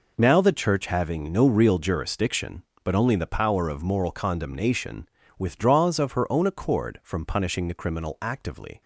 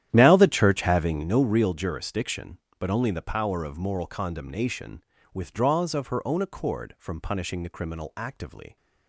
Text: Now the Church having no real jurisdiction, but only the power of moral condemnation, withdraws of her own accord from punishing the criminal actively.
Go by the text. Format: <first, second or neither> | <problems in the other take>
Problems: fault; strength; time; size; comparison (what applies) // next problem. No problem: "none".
first | starts louder than the rest; strong; until 1.4 s; 11 dB